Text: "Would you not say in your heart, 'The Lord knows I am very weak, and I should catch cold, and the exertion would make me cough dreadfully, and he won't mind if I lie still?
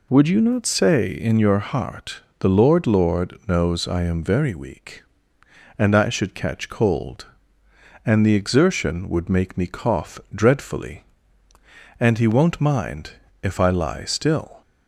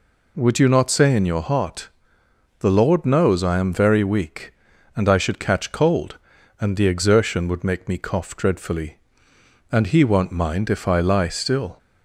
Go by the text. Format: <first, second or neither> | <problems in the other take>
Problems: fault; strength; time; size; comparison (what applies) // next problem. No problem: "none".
second | says "Lord" twice; at 2.8 s // pauses between "mind" and "if"; slight; at 13.1 s; 0.32 s long